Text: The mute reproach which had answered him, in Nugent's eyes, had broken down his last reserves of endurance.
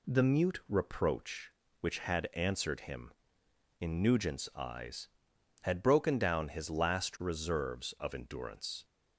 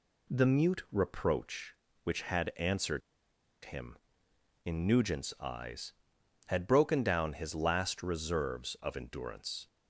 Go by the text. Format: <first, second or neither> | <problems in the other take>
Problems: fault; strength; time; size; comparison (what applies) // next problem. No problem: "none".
first | pauses between "answered" and "him"; noticeable; at 3.0 s; 0.64 s long